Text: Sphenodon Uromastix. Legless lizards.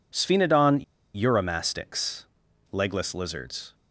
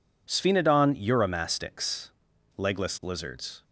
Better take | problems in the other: second | pauses between "Sphenodon" and "Uromastix"; slight; at 0.8 s; 0.31 s long

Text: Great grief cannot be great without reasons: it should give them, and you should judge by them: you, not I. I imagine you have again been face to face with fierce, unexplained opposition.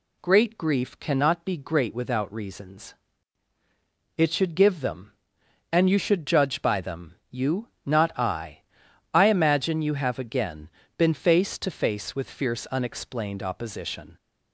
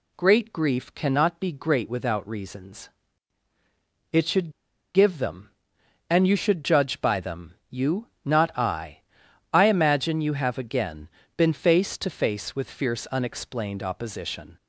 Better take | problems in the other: first | pauses between "should" and "give"; at 4.5 s; 0.43 s long // pauses between "again" and "been"; slight; at 11.0 s; 0.28 s long; slight in the first

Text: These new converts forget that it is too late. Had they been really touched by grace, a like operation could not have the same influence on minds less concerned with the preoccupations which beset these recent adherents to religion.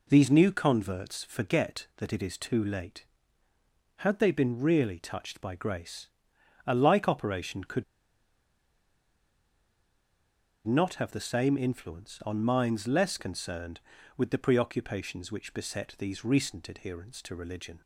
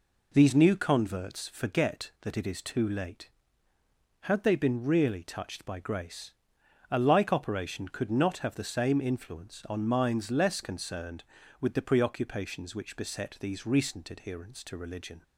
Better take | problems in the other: second | pauses between "could" and "not"; strong; at 7.8 s; 2.8 s long

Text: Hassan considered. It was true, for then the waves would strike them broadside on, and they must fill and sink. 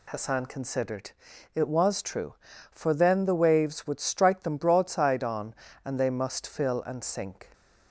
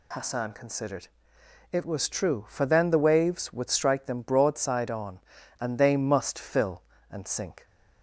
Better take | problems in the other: neither | none

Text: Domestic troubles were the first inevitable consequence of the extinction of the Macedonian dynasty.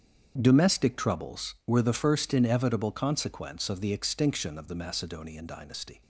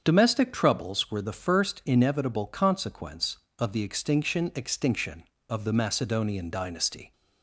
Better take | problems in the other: first | starts louder than the rest; strong; until 1.0 s; 7 dB; strong in the first // says "extinction" twice; at 4.5 s

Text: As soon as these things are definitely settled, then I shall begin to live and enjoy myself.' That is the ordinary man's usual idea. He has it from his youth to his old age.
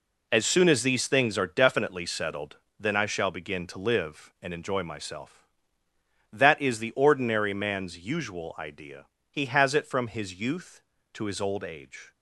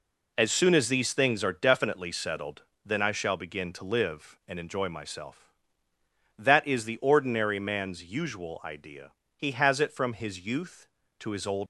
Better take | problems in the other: first | stops before "age"; at 11.6 s

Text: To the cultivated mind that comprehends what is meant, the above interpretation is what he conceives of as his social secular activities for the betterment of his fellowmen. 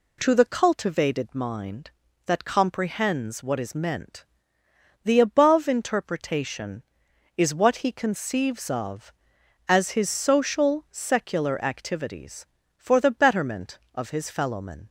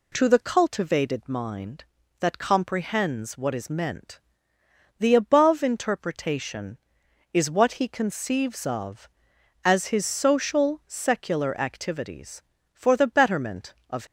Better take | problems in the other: first | stops before "his fellowmen"; at 14.0 s

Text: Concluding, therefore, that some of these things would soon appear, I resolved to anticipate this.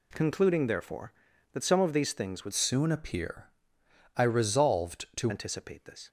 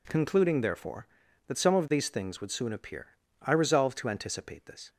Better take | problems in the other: second | changes voice from "soon" to "to"; from 2.5 to 5.3 s; 2.8 s long

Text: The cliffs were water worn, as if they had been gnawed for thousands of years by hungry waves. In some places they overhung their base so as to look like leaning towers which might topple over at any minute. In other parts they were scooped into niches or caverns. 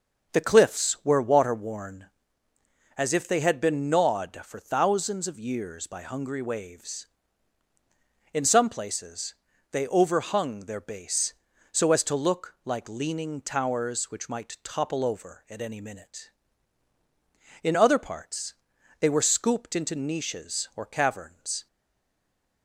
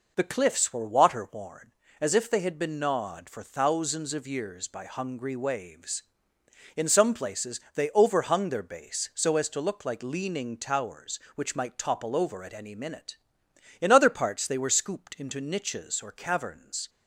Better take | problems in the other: second | starts louder than the rest; until 1.3 s; 7 dB // pauses between "places" and "they"; at 9.3 s; 0.38 s long // pauses between "parts" and "they"; noticeable; at 18.5 s; 0.46 s long // stays silent after the last word; from 21.6 s on; 1.0 s long

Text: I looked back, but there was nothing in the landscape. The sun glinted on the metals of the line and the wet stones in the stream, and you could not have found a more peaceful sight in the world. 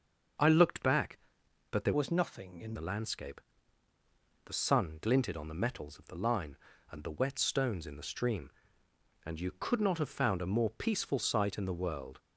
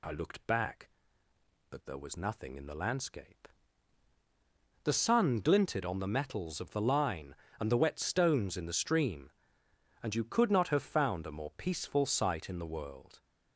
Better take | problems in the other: second | starts louder than the rest; until 1.9 s; 6.5 dB // changes voice from "was" to "in"; from 1.9 to 2.7 s; 0.8 s long

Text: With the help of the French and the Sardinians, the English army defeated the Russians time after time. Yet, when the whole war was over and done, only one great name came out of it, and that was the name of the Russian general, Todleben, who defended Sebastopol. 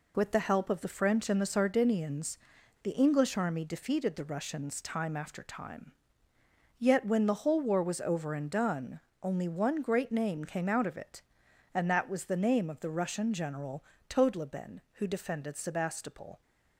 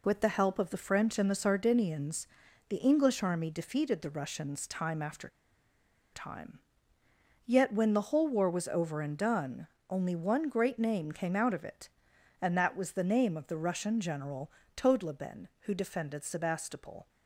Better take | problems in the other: first | pauses between "after" and "time"; noticeable; at 5.2 s; 0.83 s long

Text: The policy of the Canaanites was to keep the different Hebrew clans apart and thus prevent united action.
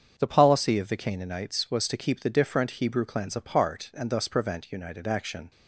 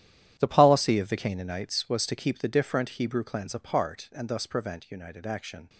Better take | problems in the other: first | gets quieter; strong; throughout; 14 dB // starts louder than the rest; strong; until 1.3 s; 11.5 dB; strong in the first

